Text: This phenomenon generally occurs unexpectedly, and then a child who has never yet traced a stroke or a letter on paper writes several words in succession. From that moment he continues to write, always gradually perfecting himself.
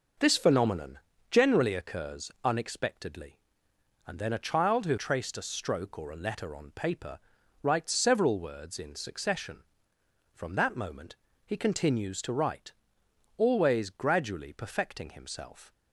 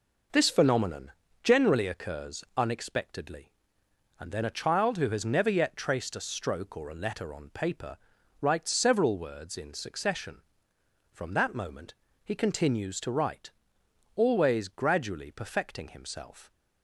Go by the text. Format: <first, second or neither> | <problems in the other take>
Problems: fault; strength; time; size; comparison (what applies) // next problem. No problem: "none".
second | pauses between "phenomenon" and "generally"; slight; at 0.9 s; 0.32 s long; slight in the second // skips "has never yet"; at 4.9 s // pauses between "paper" and "writes"; at 7.1 s; 0.42 s long; also in the second // pauses between "moment" and "he"; slight; at 11.1 s; 0.28 s long; slight in the second